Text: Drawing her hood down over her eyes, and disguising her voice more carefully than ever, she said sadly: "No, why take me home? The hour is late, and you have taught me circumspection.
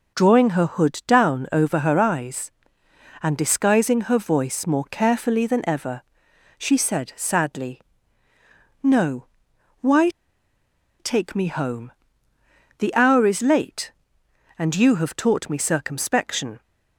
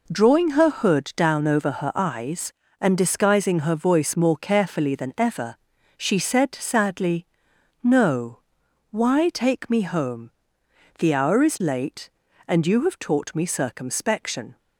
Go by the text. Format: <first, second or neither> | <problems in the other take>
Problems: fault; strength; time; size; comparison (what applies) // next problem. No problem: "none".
second | pauses between "why" and "take"; noticeable; at 10.0 s; 0.90 s long